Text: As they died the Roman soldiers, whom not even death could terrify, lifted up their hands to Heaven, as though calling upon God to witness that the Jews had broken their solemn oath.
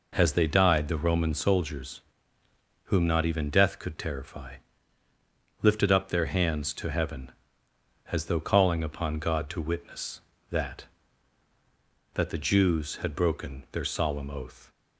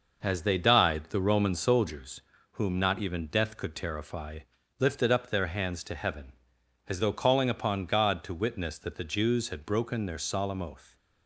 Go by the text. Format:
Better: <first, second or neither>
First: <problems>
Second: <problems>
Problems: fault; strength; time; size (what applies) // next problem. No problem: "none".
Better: second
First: says "that" twice; at 12.1 s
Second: none